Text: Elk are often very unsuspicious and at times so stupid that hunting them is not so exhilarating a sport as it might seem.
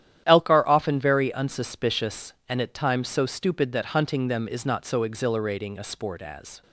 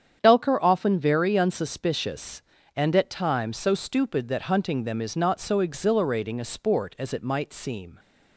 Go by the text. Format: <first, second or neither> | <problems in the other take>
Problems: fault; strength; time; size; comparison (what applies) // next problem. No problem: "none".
second | starts louder than the rest; strong; until 1.2 s; 10.5 dB; strong in the second // stops before "it might seem"; at 6.6 s